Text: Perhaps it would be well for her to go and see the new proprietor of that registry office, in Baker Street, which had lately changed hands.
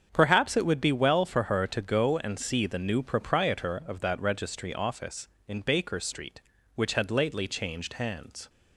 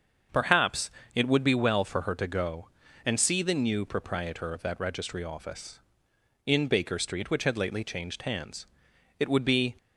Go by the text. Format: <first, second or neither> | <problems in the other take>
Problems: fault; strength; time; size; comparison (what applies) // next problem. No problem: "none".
first | starts louder than the rest; until 1.5 s; 6.5 dB; strong in the first // pauses between "Perhaps" and "it"; slight; at 0.9 s; 0.24 s long // goes on to say "It would be"; from 9.1 s on; 0.56 s long